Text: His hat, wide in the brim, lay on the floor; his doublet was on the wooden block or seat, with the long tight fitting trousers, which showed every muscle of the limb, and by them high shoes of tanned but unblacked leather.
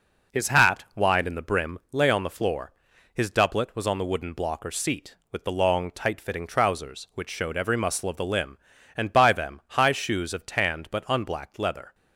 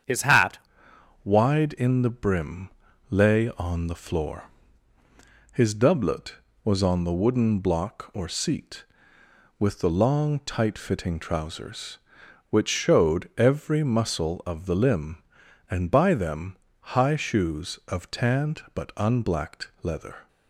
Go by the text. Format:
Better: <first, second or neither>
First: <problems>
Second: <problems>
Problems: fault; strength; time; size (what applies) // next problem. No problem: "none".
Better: first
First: none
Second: starts louder than the rest; strong; until 1.7 s; 8 dB // changes voice at "wide"; from 1.2 s on; 19.0 s long // pauses between "them" and "high"; slight; at 16.5 s; 0.36 s long